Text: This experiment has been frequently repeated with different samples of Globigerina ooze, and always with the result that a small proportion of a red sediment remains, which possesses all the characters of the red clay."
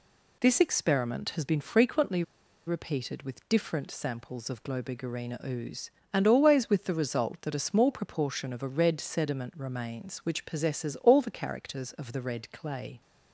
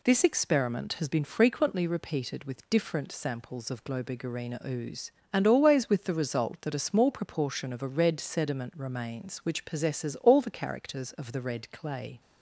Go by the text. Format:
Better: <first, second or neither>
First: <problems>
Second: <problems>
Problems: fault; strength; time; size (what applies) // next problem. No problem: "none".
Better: second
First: pauses between "frequently" and "repeated"; at 2.2 s; 0.44 s long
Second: none